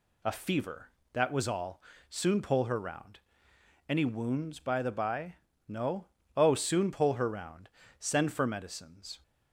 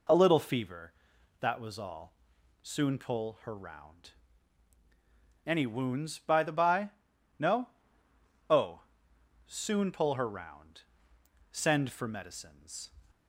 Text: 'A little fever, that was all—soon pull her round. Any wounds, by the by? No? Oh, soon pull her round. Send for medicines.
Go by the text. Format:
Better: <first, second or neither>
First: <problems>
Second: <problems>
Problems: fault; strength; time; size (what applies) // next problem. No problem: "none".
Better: second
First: skips "little"; at 0.3 s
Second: none